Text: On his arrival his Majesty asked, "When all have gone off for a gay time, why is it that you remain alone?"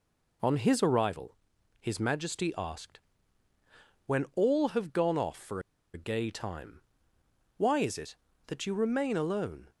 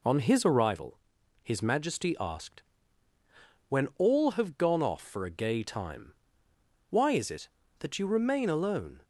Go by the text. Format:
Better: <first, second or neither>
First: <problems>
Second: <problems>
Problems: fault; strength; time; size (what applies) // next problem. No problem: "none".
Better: second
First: pauses between "arrival" and "his"; at 1.3 s; 0.44 s long // pauses between "for" and "a"; slight; at 5.6 s; 0.33 s long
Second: pauses between "arrival" and "his"; at 0.9 s; 0.44 s long